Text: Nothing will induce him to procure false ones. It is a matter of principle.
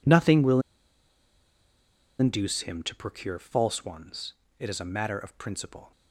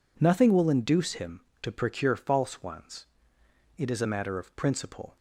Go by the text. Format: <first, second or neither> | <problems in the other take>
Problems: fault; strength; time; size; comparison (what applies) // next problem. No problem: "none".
second | pauses between "will" and "induce"; strong; at 0.5 s; 1.5 s long